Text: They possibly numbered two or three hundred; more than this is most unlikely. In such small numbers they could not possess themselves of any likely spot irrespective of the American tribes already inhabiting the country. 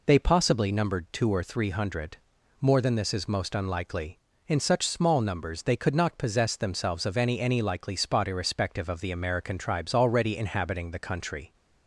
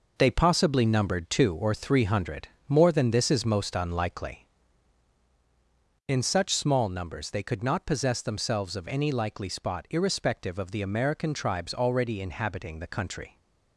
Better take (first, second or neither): second